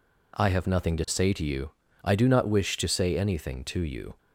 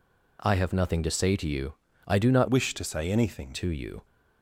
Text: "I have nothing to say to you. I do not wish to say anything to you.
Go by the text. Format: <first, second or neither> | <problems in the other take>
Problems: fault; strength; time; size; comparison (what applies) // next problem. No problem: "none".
first | changes voice from "wish" to "anything"; from 2.4 to 3.5 s; 1.1 s long